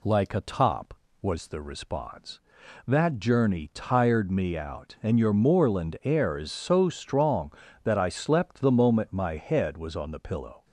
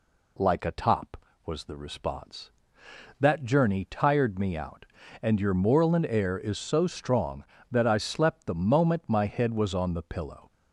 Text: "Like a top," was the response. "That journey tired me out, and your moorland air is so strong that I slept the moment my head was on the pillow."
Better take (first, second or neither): neither